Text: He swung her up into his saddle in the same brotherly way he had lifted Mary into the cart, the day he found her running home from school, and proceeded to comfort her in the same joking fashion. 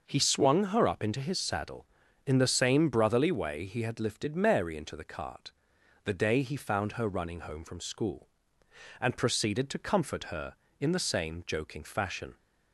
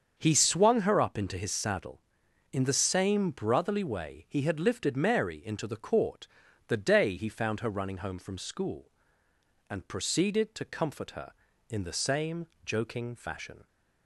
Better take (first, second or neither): first